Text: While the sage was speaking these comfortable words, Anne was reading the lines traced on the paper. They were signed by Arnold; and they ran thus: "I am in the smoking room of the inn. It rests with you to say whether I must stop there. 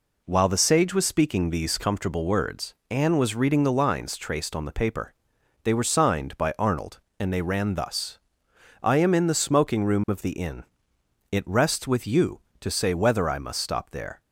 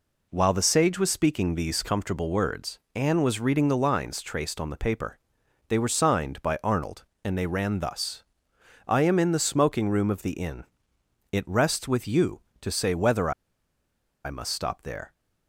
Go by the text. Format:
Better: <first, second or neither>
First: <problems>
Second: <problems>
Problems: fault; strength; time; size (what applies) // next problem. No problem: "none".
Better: first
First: none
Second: pauses between "whether" and "I"; noticeable; at 13.3 s; 0.94 s long